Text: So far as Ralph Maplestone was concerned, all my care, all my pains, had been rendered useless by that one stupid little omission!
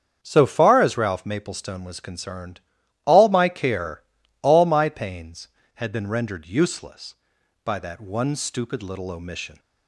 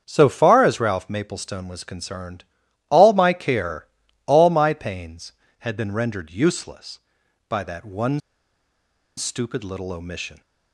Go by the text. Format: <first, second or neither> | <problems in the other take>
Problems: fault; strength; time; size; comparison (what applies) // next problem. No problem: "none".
first | starts louder than the rest; strong; until 1.0 s; 7.5 dB; strong in the first // pauses between "one" and "stupid"; noticeable; at 8.1 s; 0.97 s long